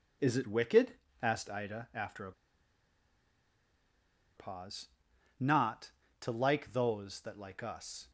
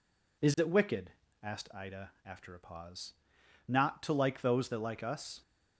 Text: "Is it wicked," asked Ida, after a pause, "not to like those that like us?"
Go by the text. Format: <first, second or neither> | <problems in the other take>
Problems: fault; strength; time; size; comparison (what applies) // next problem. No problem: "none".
second | pauses between "a" and "pause"; strong; at 2.3 s; 2.0 s long